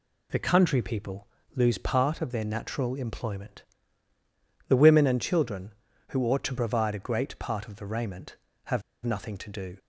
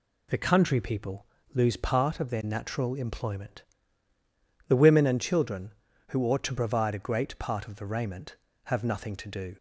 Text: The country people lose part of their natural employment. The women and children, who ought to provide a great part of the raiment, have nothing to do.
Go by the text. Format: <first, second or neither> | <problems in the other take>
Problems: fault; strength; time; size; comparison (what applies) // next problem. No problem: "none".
second | pauses between "people" and "lose"; slight; at 1.2 s; 0.30 s long; slight in the second // pauses between "have" and "nothing"; slight; at 8.8 s; 0.24 s long